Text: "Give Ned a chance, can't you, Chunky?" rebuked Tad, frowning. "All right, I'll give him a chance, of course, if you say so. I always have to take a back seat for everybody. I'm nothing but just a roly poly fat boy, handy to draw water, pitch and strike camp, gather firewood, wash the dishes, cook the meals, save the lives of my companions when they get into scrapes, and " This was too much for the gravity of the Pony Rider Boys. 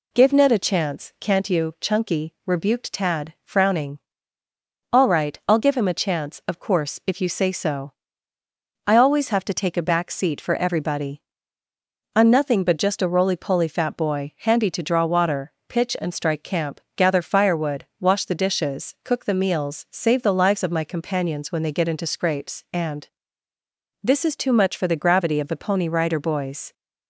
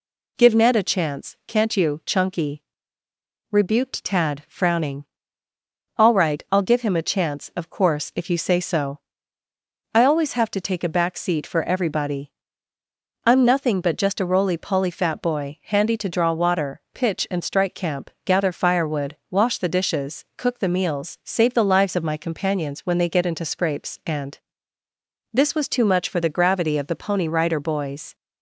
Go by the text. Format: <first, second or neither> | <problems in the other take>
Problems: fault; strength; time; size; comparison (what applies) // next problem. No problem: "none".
second | says "is" for "was"; at 24.2 s